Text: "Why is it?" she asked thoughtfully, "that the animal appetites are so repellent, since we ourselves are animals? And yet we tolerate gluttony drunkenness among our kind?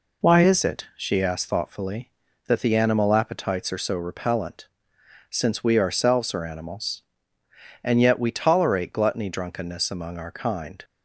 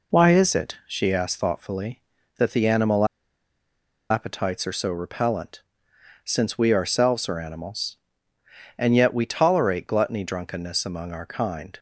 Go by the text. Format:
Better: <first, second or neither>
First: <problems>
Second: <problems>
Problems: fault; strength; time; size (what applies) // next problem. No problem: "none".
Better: first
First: none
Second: pauses between "animal" and "appetites"; at 3.0 s; 1.0 s long